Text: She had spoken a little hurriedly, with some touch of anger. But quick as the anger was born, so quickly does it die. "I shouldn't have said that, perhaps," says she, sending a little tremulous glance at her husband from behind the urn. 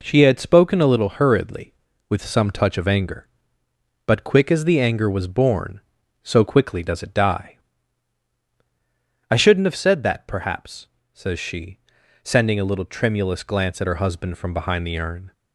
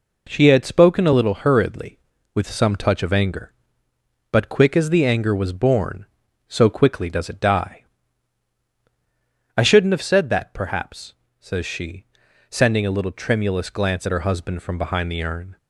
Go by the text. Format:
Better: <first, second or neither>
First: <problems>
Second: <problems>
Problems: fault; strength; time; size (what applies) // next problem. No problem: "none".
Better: neither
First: none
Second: none